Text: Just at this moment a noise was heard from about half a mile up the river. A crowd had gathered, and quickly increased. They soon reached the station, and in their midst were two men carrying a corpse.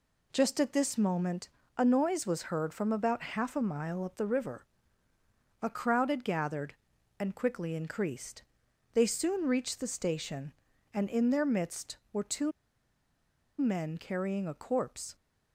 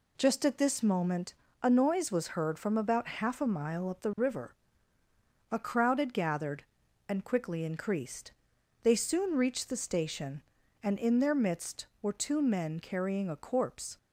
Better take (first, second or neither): second